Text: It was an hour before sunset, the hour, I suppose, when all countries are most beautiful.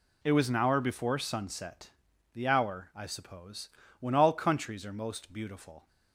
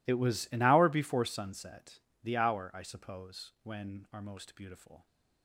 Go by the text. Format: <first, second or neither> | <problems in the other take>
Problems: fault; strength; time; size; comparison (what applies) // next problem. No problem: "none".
first | skips "all countries"; at 4.0 s